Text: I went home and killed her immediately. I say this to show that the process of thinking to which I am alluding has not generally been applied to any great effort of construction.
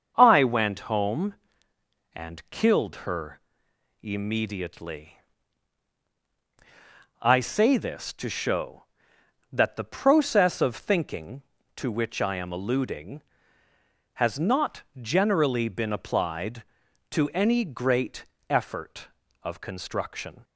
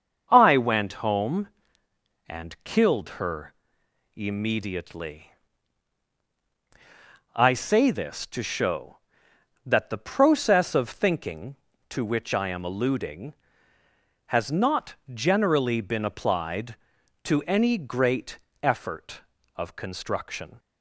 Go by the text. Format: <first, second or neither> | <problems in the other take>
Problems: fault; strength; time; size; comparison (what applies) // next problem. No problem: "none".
neither | starts louder than the rest; the same in both // pauses between "her" and "immediately"; noticeable; the same in both // pauses between "not" and "generally"; slight; the same in both // pauses between "great" and "effort"; slight; the same in both